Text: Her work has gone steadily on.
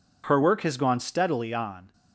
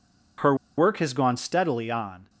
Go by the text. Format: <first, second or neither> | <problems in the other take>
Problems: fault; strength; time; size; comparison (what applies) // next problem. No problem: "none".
first | pauses between "Her" and "work"; slight; at 0.5 s; 0.22 s long